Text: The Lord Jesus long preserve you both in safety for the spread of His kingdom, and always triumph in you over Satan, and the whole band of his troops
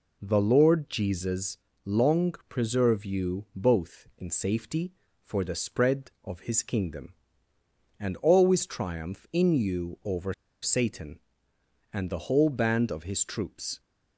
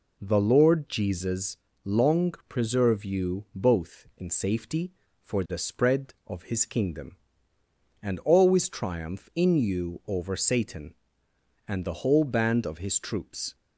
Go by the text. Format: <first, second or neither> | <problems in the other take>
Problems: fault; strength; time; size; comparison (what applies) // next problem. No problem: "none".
second | pauses between "Jesus" and "long"; slight; at 1.5 s; 0.26 s long; slight in the second // pauses between "over" and "Satan"; slight; at 10.3 s; 0.28 s long